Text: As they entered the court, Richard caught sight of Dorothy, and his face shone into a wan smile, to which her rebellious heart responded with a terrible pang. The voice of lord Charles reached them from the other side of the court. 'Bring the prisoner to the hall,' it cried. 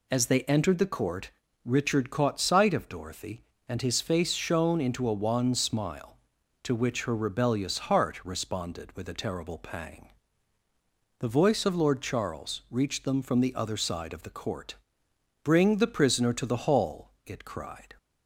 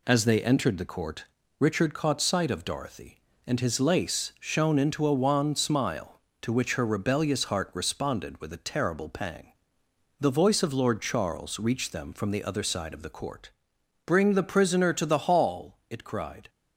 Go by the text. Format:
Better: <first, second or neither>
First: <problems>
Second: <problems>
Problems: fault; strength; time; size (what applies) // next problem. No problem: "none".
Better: first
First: none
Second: says "lace" for "face"; at 3.7 s